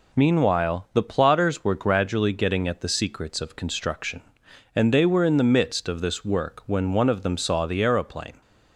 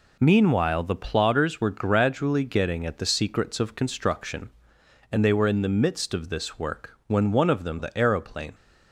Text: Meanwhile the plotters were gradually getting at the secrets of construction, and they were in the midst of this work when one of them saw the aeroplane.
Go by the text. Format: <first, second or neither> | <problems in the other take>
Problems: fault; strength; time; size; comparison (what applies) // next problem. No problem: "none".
first | skips "saw"; at 7.7 s